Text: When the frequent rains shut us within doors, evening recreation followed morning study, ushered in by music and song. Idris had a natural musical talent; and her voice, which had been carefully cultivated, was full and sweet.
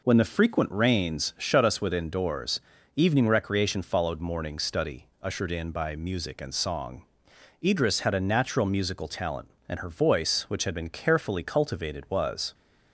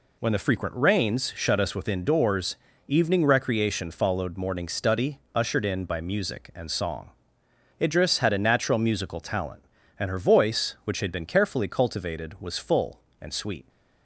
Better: second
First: stops before "full and sweet"; at 12.5 s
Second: none

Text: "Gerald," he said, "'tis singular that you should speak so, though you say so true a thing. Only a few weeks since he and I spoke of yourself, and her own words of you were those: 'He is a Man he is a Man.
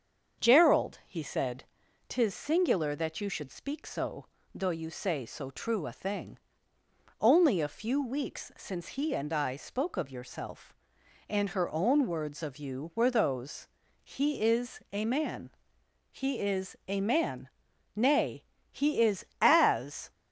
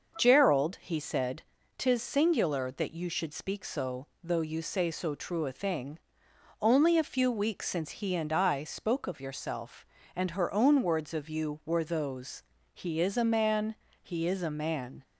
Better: second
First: starts louder than the rest; until 1.4 s; 7 dB // pauses between "Man" and "he"; noticeable; at 15.5 s; 0.62 s long // goes on to say "Nay he is as"; strong; from 17.9 s on; 2.1 s long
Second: starts louder than the rest; until 1.1 s; 6 dB // pauses between "Man" and "he"; slight; at 13.7 s; 0.30 s long

